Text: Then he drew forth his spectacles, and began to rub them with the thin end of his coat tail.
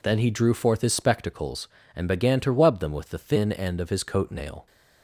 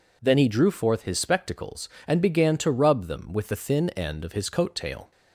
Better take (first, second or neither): second